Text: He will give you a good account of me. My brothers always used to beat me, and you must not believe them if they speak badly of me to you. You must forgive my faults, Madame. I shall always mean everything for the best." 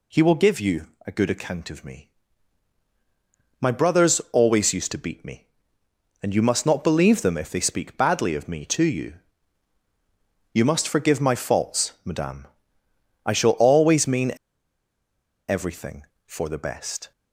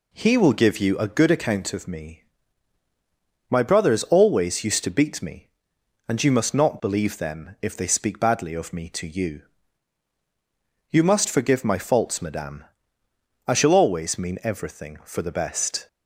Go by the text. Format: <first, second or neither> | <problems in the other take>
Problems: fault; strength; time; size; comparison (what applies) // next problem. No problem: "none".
second | pauses between "you" and "a"; slight; at 0.8 s; 0.18 s long // pauses between "mean" and "everything"; at 14.3 s; 1.1 s long